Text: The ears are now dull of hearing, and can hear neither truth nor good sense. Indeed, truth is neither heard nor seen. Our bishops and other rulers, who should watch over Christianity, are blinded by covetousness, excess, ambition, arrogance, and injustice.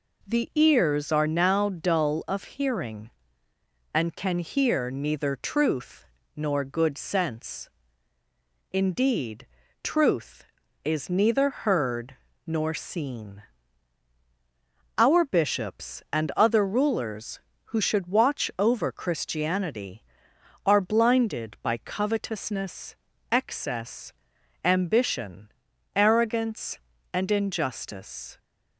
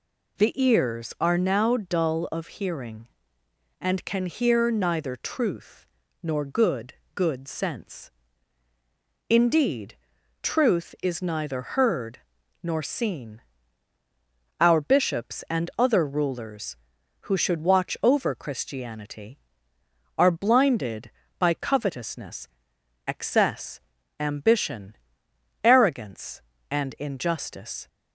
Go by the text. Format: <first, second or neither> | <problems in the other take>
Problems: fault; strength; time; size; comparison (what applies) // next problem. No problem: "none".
first | pauses between "truth" and "nor"; slight; at 5.8 s; 0.36 s long; slight in the first // says "good" twice; at 7.1 s // pauses between "heard" and "nor"; at 12.1 s; 0.44 s long; slight in the first